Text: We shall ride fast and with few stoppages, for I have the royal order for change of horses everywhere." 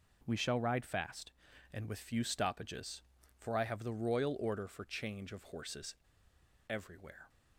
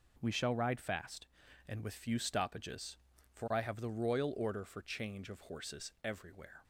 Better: second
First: pauses between "horses" and "everywhere"; noticeable; at 5.9 s; 0.74 s long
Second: none

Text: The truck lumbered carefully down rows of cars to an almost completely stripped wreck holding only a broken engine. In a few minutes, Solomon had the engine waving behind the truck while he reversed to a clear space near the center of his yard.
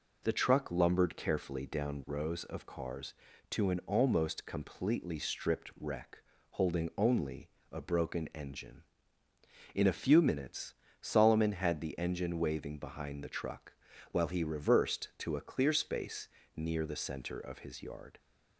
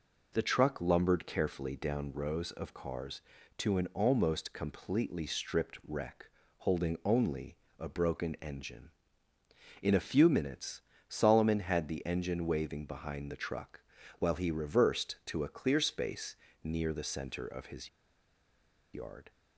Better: first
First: pauses between "wreck" and "holding"; slight; at 6.1 s; 0.32 s long // pauses between "only" and "a"; slight; at 7.4 s; 0.22 s long // pauses between "truck" and "while"; slight; at 13.7 s; 0.36 s long // pauses between "space" and "near"; slight; at 16.2 s; 0.30 s long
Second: pauses between "wreck" and "holding"; slight; at 6.2 s; 0.32 s long // pauses between "only" and "a"; slight; at 7.5 s; 0.22 s long // pauses between "truck" and "while"; slight; at 13.8 s; 0.36 s long // pauses between "space" and "near"; slight; at 16.3 s; 0.30 s long // pauses between "his" and "yard"; at 17.8 s; 1.0 s long

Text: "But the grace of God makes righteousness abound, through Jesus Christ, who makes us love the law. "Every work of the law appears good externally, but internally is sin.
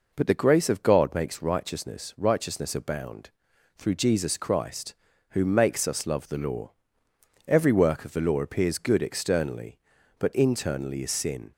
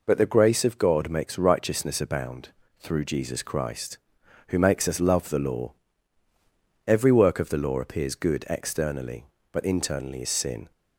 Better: second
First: says "righteousness" twice; at 2.1 s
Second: none

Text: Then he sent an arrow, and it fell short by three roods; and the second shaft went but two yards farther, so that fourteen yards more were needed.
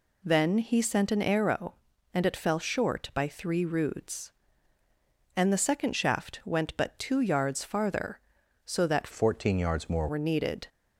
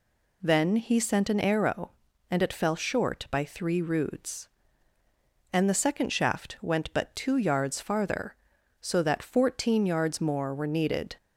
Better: second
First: changes voice from "fourteen" to "more"; from 9.1 to 10.0 s; 0.9 s long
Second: none

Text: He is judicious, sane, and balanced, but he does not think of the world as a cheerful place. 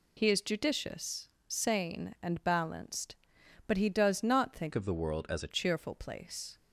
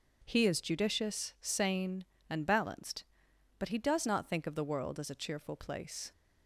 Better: second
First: changes voice from "of" to "a"; from 4.7 to 5.5 s; 0.8 s long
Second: none

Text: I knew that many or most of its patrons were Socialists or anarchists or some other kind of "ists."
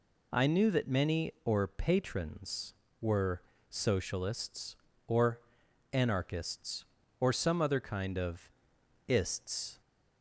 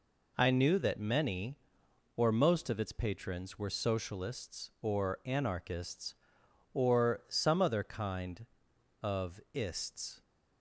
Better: second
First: skips "most of its"; at 1.6 s // pauses between "were" and "Socialists"; slight; at 3.4 s; 0.28 s long // pauses between "or" and "anarchists"; noticeable; at 5.4 s; 0.52 s long // pauses between "of" and "ists"; noticeable; at 8.4 s; 0.60 s long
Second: none

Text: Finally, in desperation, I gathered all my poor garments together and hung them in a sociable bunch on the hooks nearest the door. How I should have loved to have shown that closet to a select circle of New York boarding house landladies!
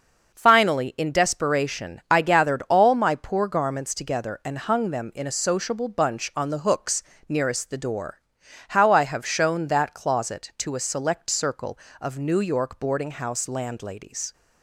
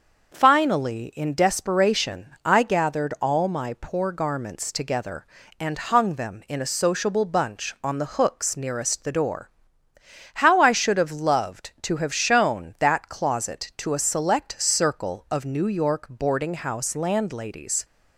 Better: second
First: starts louder than the rest; until 1.4 s; 6 dB // pauses between "hooks" and "nearest"; slight; at 7.0 s; 0.26 s long // skips "should have loved to"; at 9.0 s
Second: starts louder than the rest; noticeable; until 1.3 s; 6 dB

